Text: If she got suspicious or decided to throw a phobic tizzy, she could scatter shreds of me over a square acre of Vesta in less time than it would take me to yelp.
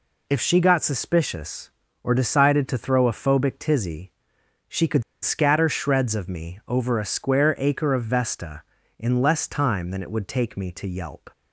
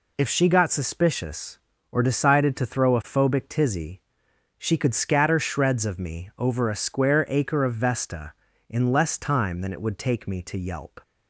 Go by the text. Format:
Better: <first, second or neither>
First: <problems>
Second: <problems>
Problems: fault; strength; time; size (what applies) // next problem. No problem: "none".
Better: second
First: pauses between "could" and "scatter"; slight; at 5.0 s; 0.20 s long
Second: none